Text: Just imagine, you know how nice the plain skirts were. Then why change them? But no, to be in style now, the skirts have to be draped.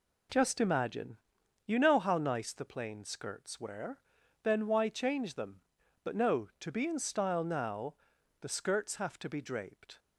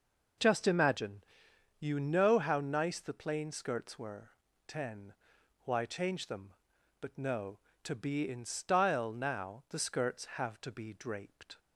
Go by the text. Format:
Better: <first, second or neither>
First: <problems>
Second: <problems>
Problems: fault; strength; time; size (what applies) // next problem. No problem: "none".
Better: first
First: none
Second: says "Ten" for "Then"; at 4.6 s